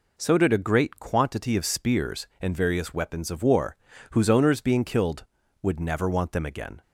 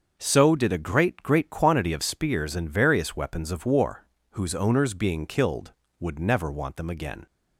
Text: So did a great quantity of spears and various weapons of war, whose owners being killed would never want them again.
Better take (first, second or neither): first